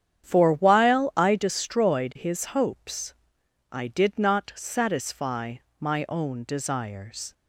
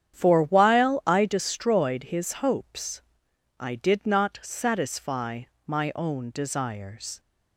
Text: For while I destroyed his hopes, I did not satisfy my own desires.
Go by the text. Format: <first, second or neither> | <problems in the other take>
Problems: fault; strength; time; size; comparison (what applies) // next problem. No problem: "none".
neither | starts louder than the rest; strong; the same in both // pauses between "satisfy" and "my"; slight; the same in both